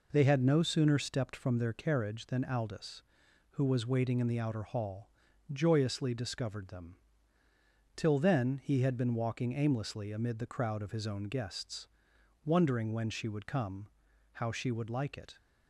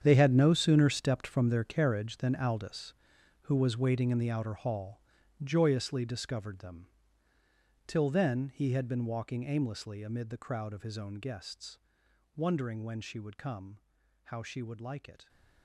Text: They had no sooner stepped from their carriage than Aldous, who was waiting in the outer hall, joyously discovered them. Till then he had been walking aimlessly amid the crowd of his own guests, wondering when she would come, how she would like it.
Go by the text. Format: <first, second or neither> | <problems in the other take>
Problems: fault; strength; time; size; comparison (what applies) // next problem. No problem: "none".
first | gets quieter; strong; throughout; 13.5 dB